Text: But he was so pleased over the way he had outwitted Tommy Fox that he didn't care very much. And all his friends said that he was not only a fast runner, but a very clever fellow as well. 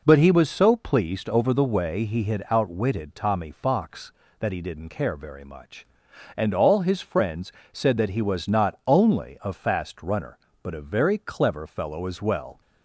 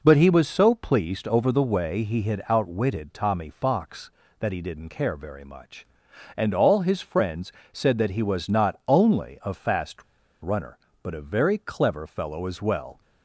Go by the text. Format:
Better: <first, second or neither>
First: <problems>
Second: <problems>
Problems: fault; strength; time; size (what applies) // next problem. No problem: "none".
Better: first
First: pauses between "friends" and "said"; slight; at 7.5 s; 0.20 s long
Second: pauses between "friends" and "said"; slight; at 7.5 s; 0.20 s long // pauses between "fast" and "runner"; at 10.0 s; 0.39 s long